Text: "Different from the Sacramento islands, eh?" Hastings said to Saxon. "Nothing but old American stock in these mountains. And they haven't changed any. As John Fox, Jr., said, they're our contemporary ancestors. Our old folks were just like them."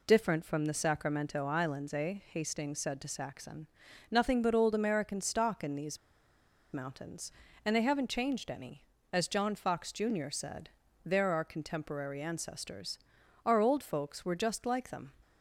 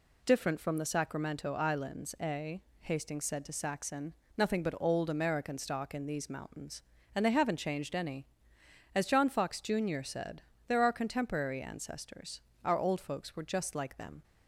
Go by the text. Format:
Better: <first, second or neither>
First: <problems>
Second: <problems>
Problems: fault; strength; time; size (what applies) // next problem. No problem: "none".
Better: second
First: pauses between "these" and "mountains"; noticeable; at 5.9 s; 0.75 s long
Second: none